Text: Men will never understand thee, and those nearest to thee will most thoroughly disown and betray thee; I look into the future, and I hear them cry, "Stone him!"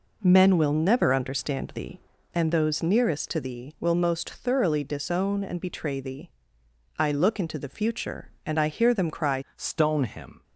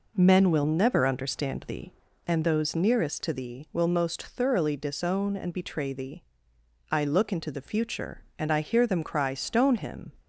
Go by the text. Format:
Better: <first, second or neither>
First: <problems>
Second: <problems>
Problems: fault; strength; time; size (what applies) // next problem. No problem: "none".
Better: second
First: changes voice at "Stone"; from 9.5 s on; 0.9 s long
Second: none